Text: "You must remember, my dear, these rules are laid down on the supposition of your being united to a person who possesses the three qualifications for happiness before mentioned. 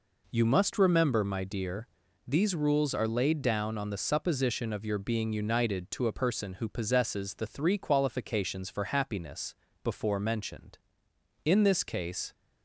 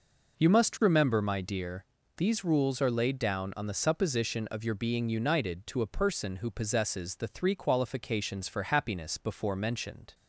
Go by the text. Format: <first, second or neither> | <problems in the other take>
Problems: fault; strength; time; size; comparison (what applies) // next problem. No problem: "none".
second | pauses between "happiness" and "before"; slight; at 9.5 s; 0.28 s long // goes on to say "In this case"; noticeable; from 11.4 s on; 0.88 s long